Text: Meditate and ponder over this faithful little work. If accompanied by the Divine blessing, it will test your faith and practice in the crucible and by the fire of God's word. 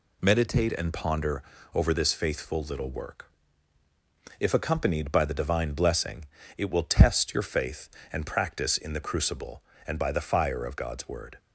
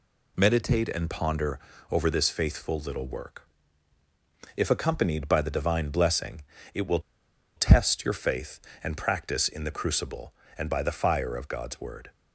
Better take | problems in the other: first | pauses between "ponder" and "over"; slight; at 1.5 s; 0.32 s long; slight in the first // pauses between "will" and "test"; noticeable; at 7.0 s; 0.56 s long

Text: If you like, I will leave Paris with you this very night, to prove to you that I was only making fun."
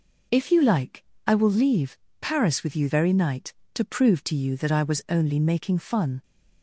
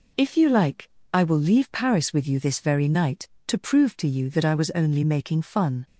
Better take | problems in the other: second | pauses between "leave" and "Paris"; slight; at 1.9 s; 0.22 s long // skips "this"; at 2.8 s

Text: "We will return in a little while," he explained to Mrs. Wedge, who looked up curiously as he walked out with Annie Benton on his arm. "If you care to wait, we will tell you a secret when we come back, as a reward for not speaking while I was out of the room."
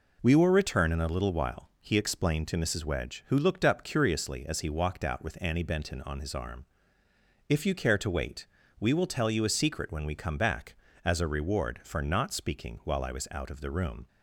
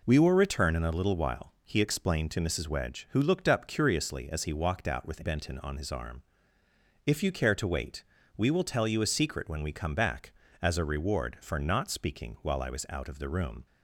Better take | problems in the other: first | skips "Annie"; at 5.2 s

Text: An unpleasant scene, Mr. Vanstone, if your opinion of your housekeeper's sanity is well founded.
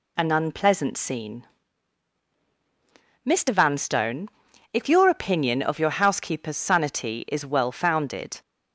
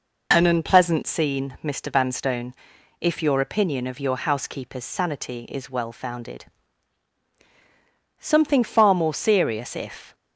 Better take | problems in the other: first | goes on to say "Something far more serious if"; strong; from 8.1 s on; 1.9 s long

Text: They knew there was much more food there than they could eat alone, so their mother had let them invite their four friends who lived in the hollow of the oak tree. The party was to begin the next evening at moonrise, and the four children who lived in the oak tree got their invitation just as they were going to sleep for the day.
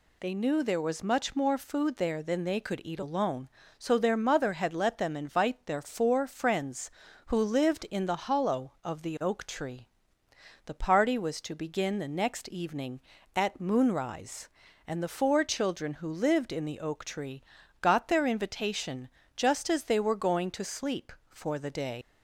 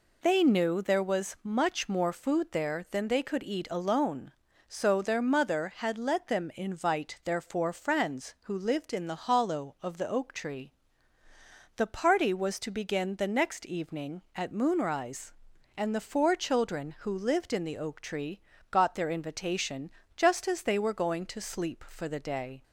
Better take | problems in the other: second | pauses between "tree" and "got"; at 17.4 s; 0.38 s long; slight in the second // pauses between "invitation" and "just"; slight; at 19.0 s; 0.28 s long; slight in the second // leaves "day" unfinished; at 22.0 s; 100 ms

